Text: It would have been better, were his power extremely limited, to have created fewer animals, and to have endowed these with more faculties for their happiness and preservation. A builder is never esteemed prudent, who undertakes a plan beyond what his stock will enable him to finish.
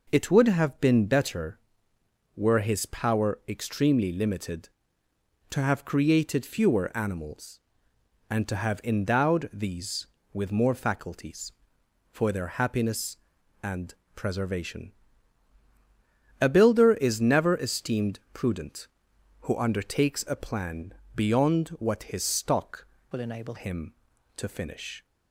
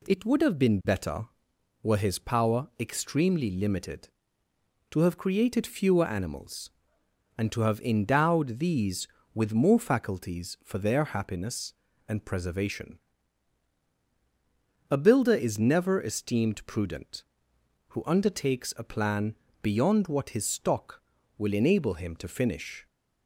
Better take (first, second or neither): second